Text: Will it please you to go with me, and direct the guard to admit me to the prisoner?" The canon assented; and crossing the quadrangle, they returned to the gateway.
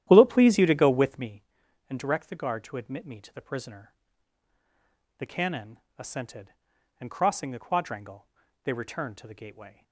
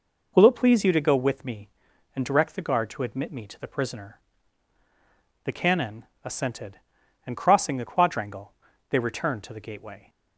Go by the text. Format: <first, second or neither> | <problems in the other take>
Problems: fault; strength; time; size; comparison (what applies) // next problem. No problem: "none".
second | starts louder than the rest; strong; until 1.3 s; 11.5 dB // pauses between "canon" and "assented"; slight; at 5.7 s; 0.18 s long; slight in the second